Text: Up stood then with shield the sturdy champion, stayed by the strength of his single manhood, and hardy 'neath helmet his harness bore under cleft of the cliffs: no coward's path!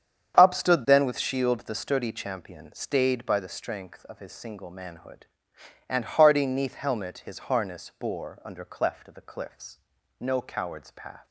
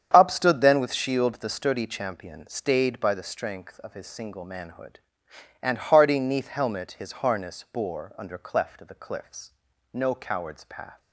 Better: neither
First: starts louder than the rest; strong; until 1.4 s; 8 dB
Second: starts louder than the rest; strong; until 1.1 s; 8.5 dB

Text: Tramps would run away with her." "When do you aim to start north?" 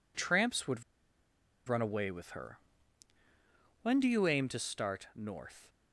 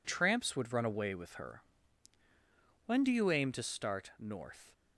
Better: second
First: pauses between "would" and "run"; noticeable; at 0.8 s; 0.85 s long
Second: none

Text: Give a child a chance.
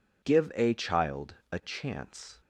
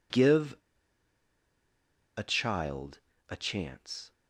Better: first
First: pauses between "child" and "a"; slight; at 1.3 s; 0.16 s long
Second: pauses between "Give" and "a"; strong; at 0.5 s; 1.5 s long // pauses between "child" and "a"; slight; at 2.9 s; 0.28 s long

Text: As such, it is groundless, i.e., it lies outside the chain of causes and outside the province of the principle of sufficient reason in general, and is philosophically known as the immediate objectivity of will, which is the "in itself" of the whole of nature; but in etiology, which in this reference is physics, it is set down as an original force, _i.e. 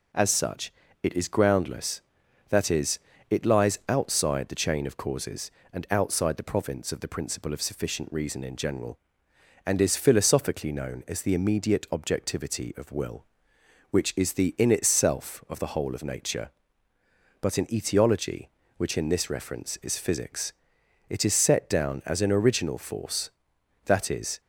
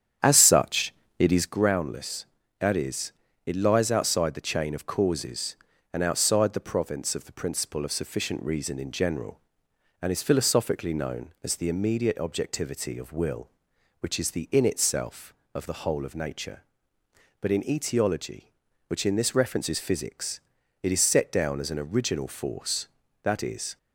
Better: first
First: none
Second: starts louder than the rest; strong; until 1.5 s; 9 dB

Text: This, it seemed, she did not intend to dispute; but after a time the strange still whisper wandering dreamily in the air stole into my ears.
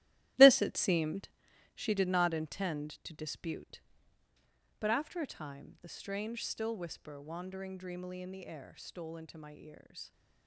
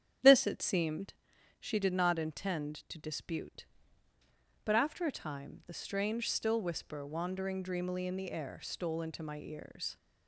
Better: second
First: gets quieter; strong; throughout; 10.5 dB // starts louder than the rest; strong; until 1.8 s; 15 dB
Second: starts louder than the rest; strong; until 1.6 s; 9.5 dB

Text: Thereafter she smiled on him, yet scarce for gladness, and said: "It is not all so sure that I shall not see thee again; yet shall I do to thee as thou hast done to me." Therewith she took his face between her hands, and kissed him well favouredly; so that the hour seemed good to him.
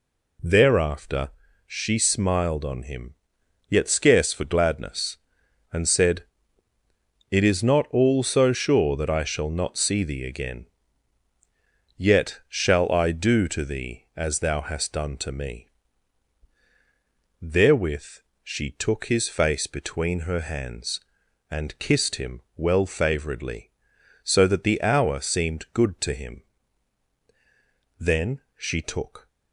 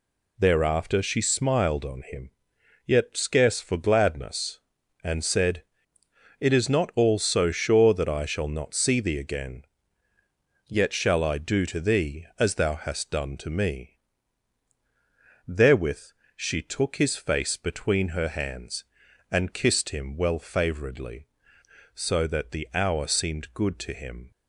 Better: second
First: pauses between "Thereafter" and "she"; at 1.2 s; 0.38 s long // pauses between "Therewith" and "she"; slight; at 18.1 s; 0.22 s long // pauses between "him" and "well"; slight; at 22.3 s; 0.16 s long // goes on to say "Then she took"; noticeable; from 27.9 s on; 1.2 s long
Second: pauses between "Therewith" and "she"; slight; at 16.1 s; 0.24 s long

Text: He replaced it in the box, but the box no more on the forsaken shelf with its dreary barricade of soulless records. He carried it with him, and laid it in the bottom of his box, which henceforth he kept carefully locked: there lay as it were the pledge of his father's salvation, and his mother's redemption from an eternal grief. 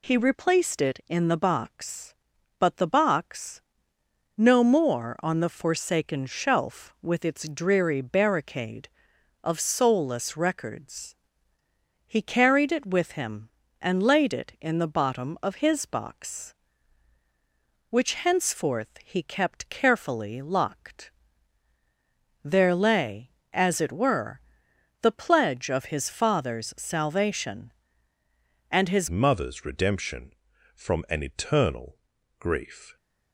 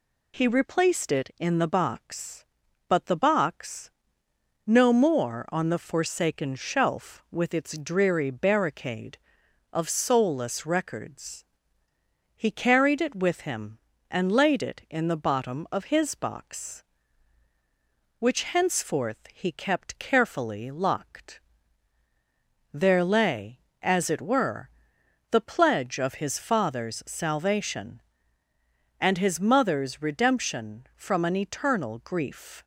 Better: second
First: pauses between "box" and "no"; noticeable; at 3.6 s; 0.74 s long // pauses between "were" and "the"; noticeable; at 24.3 s; 0.62 s long // changes voice at "mother's"; from 29.0 s on; 3.9 s long // pauses between "eternal" and "grief"; at 31.9 s; 0.44 s long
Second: pauses between "box" and "no"; noticeable; at 3.9 s; 0.74 s long // pauses between "were" and "the"; noticeable; at 24.6 s; 0.62 s long

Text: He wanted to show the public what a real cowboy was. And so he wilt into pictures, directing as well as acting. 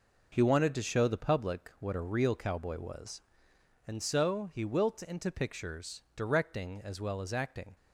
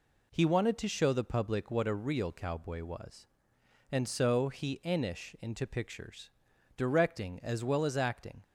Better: first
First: none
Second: says "enish" for "wilt"; at 4.8 s

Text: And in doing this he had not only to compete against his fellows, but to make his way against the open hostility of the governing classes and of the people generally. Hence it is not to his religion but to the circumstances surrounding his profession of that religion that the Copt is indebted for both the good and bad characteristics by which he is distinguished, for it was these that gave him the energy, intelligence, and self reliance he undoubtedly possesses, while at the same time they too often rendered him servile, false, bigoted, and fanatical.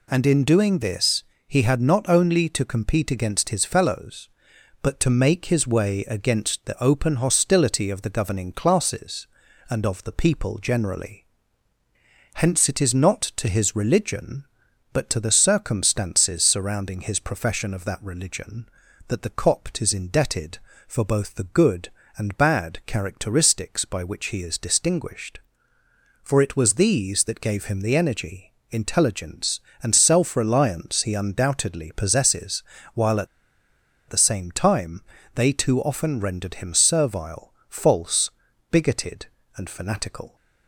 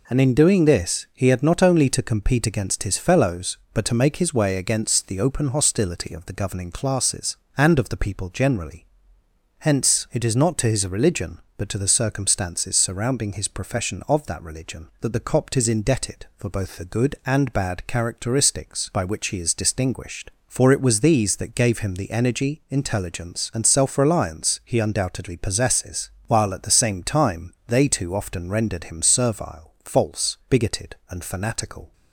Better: second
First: pauses between "this" and "he"; slight; at 1.2 s; 0.24 s long // pauses between "at" and "the"; noticeable; at 33.2 s; 0.82 s long // pauses between "time" and "they"; slight; at 35.0 s; 0.34 s long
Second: none

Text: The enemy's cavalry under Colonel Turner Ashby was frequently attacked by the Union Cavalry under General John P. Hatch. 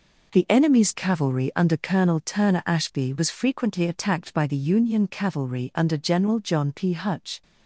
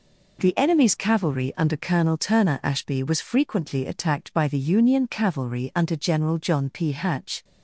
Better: second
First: says "Hutch" for "Hatch"; at 6.9 s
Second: none

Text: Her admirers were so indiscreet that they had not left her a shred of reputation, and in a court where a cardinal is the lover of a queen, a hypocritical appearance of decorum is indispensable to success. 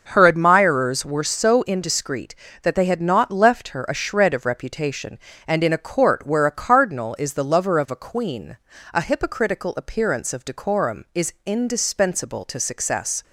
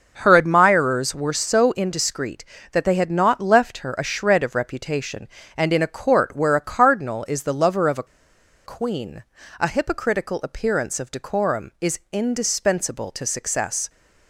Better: first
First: none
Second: pauses between "a" and "queen"; noticeable; at 8.0 s; 0.62 s long

